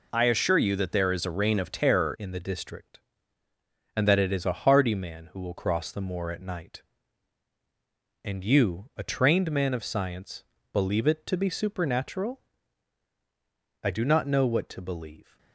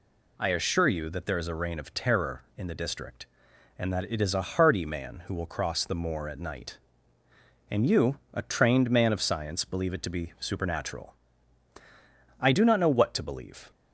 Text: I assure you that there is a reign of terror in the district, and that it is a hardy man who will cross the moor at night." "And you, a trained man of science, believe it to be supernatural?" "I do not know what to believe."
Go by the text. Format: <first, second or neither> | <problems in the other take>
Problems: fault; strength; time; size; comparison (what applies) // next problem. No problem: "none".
second | changes voice at "in"; from 2.1 s on; 13.2 s long